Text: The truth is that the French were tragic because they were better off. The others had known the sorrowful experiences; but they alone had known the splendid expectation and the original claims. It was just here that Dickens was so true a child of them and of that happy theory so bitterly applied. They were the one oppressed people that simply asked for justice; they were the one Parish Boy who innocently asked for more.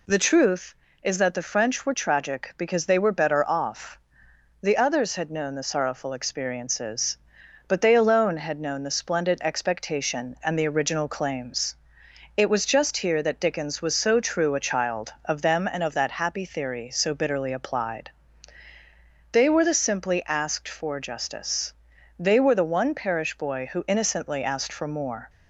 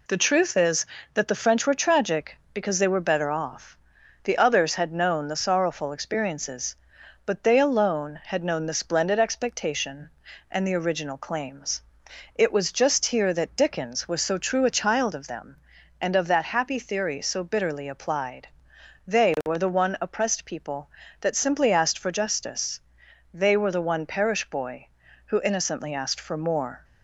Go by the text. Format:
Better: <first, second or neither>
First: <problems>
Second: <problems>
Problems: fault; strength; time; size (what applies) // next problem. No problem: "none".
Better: second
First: skips "one oppressed people that"; at 19.7 s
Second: none